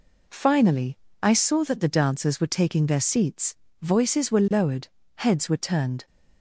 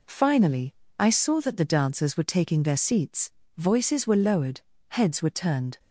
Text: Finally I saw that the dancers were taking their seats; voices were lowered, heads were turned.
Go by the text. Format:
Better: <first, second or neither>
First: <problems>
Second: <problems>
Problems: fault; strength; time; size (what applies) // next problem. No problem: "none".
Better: neither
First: pauses between "Finally" and "I"; slight; at 0.9 s; 0.24 s long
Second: pauses between "Finally" and "I"; slight; at 0.7 s; 0.24 s long